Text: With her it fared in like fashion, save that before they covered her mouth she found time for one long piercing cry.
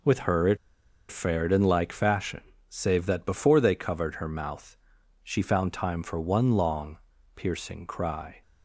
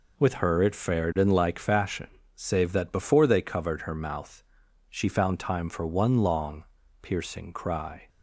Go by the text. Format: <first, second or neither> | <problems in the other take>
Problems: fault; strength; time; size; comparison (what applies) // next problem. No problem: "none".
second | pauses between "it" and "fared"; noticeable; at 0.5 s; 0.54 s long // pauses between "mouth" and "she"; noticeable; at 4.7 s; 0.48 s long; noticeable in the second // pauses between "long" and "piercing"; at 6.9 s; 0.38 s long; also in the second